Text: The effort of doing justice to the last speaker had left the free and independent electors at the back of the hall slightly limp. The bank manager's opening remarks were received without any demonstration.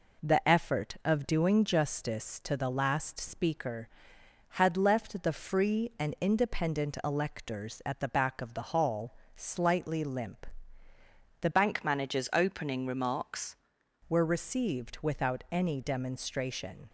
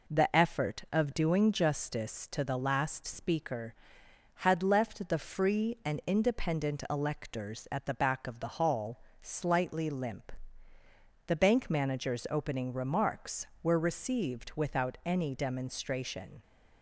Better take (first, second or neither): second